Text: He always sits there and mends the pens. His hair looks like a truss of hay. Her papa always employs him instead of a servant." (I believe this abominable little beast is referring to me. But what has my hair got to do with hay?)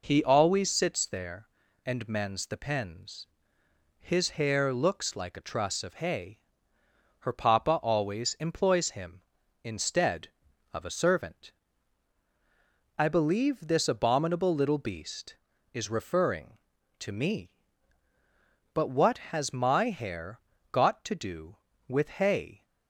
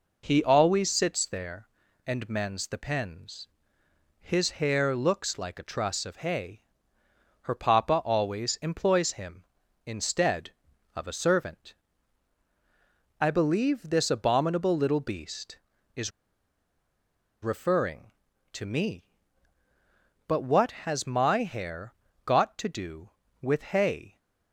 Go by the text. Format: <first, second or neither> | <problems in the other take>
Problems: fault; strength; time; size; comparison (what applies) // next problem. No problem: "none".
first | pauses between "is" and "referring"; strong; at 16.1 s; 1.3 s long // pauses between "hair" and "got"; slight; at 21.9 s; 0.32 s long; slight in the first